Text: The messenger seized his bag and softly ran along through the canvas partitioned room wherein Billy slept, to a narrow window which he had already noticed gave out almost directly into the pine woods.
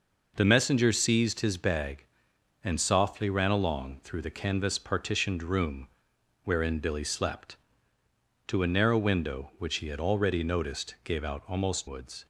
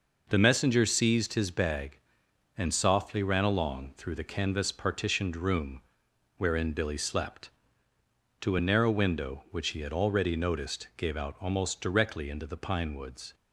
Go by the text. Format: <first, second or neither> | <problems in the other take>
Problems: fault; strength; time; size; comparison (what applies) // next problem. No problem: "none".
second | pauses between "room" and "wherein"; noticeable; at 5.8 s; 0.54 s long; noticeable in the second // skips "directly into the pine"; at 11.8 s